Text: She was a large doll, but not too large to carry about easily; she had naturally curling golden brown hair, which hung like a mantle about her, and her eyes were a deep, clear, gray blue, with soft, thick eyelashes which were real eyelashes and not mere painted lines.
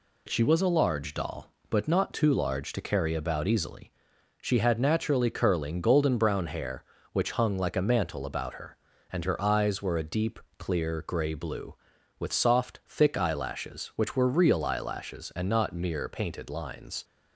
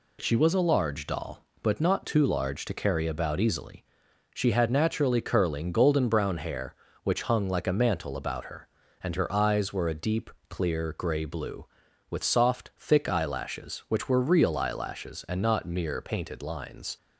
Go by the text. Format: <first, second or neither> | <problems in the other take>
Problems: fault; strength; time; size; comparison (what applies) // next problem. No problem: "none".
neither | none